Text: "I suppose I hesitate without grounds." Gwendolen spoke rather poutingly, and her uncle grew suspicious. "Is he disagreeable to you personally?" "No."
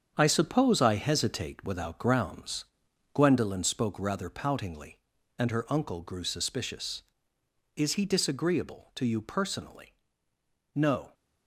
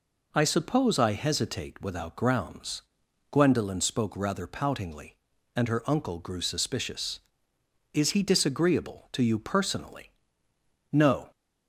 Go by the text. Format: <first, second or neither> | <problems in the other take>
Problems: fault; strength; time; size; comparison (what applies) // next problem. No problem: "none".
second | gets quieter; strong; throughout; 7.5 dB